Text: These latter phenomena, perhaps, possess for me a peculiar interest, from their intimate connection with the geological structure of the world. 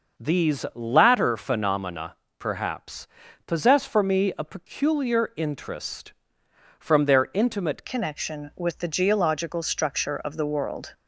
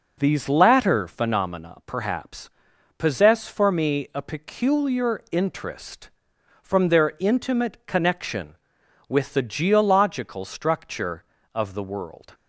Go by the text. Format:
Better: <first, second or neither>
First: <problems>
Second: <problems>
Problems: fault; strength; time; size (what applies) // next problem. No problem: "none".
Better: second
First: changes voice at "connection"; from 7.8 s on; 3.1 s long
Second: none